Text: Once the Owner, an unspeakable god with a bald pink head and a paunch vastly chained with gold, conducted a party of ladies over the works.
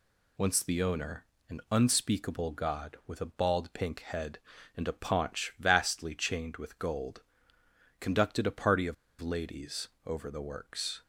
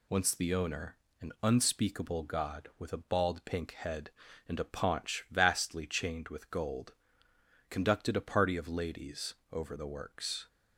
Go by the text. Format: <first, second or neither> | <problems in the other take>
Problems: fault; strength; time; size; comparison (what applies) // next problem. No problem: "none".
second | pauses between "of" and "ladies"; slight; at 8.9 s; 0.25 s long // pauses between "ladies" and "over"; slight; at 9.8 s; 0.18 s long; slight in the second